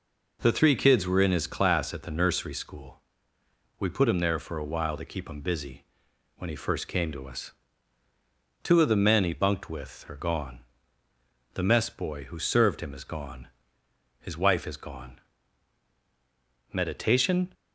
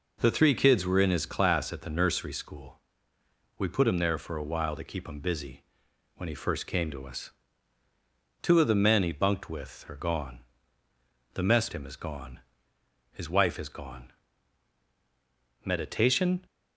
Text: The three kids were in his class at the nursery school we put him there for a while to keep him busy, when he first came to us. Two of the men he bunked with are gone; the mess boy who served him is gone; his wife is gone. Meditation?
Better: first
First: pauses between "school" and "we"; noticeable; at 2.9 s; 0.82 s long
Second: pauses between "school" and "we"; noticeable; at 2.7 s; 0.82 s long // skips "boy who served"; at 11.7 s

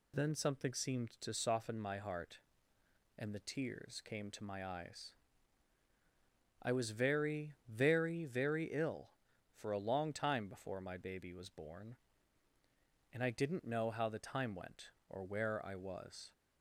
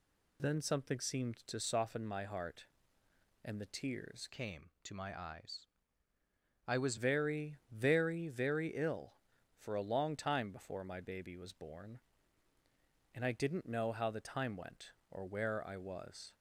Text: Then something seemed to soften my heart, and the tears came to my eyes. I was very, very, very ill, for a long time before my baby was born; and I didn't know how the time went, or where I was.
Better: first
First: none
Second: changes voice from "came" to "was"; from 4.2 to 6.9 s; 2.7 s long

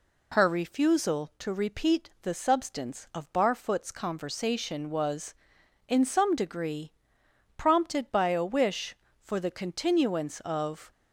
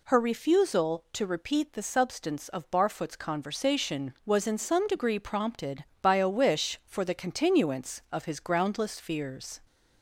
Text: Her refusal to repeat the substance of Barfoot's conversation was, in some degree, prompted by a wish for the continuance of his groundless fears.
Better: second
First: stops before "his groundless fears"; at 10.9 s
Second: none

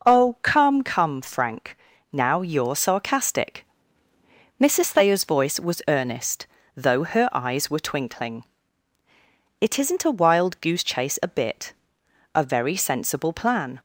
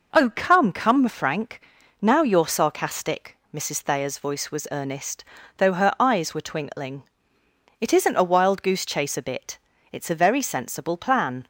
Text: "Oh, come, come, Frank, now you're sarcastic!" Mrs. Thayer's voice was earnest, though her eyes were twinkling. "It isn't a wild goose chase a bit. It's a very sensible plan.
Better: second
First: skips "It's"; at 12.0 s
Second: none

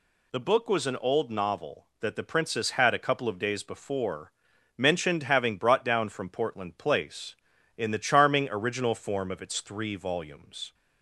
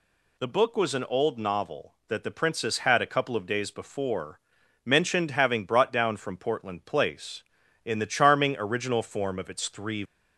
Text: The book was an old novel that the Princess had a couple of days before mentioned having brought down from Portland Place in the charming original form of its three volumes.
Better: first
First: pauses between "before" and "mentioned"; at 4.3 s; 0.44 s long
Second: pauses between "before" and "mentioned"; at 4.3 s; 0.44 s long // stops before "volumes"; at 10.0 s

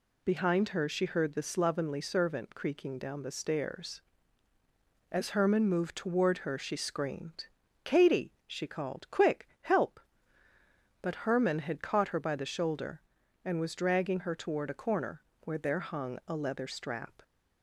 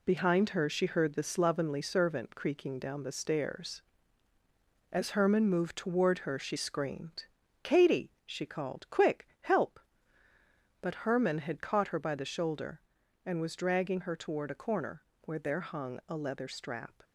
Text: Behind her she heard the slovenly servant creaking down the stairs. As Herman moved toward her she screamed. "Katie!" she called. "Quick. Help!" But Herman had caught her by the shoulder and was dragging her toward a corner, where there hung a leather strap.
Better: first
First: none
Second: gets quieter; throughout; 6.5 dB

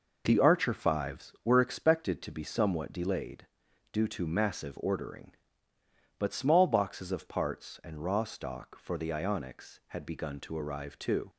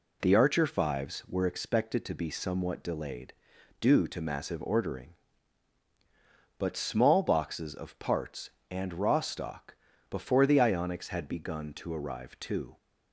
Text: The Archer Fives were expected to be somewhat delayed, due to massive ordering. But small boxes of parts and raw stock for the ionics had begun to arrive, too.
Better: first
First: none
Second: says "before" for "for"; at 10.1 s

